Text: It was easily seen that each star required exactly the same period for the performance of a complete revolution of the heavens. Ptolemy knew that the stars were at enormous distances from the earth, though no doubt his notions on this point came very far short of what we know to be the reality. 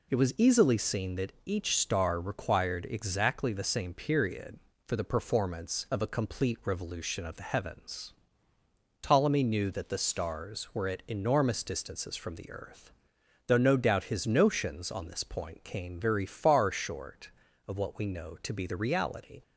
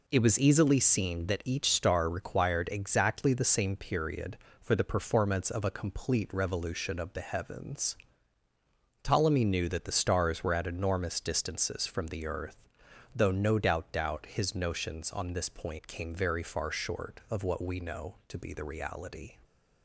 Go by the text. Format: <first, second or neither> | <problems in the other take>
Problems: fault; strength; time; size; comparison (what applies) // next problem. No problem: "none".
first | says "doubt" twice; at 13.9 s